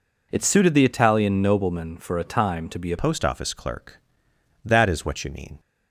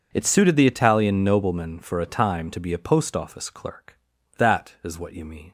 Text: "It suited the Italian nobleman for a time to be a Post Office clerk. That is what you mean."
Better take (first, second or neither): second